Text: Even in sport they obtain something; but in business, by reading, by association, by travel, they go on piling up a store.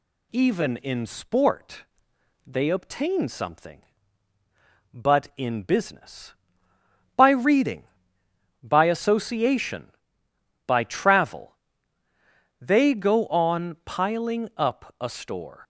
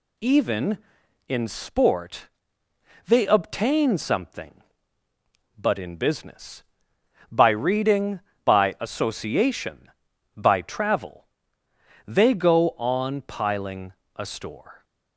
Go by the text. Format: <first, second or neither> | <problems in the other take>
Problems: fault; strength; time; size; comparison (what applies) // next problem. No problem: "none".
first | pauses between "sport" and "they"; noticeable; at 2.2 s; 0.80 s long; noticeable in the first // skips "up"; at 14.0 s